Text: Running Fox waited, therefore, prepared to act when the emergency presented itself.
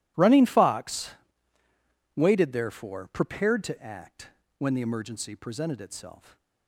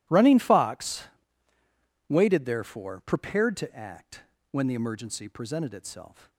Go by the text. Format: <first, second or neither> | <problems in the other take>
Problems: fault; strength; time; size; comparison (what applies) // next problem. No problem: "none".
neither | pauses between "Fox" and "waited"; the same in both // pauses between "act" and "when"; slight; the same in both